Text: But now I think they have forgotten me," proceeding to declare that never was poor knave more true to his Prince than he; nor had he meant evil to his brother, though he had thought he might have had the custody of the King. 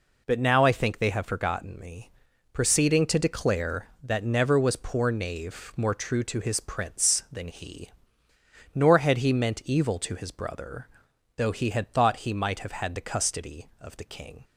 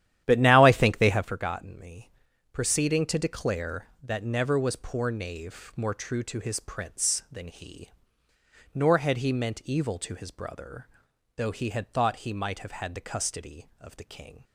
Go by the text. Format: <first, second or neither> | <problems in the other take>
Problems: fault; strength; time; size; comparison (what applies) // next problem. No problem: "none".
first | starts louder than the rest; strong; until 1.3 s; 11.5 dB